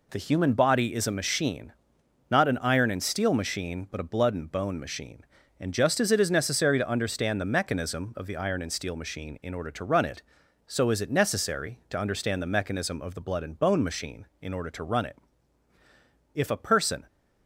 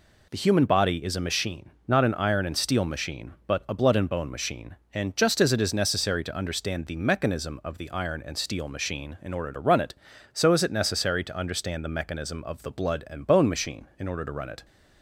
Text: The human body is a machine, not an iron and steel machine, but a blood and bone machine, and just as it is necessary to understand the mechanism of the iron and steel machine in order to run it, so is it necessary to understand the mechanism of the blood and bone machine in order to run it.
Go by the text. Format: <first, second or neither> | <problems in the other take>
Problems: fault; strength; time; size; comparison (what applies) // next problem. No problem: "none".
second | goes on to say "If a person"; noticeable; from 16.3 s on; 0.70 s long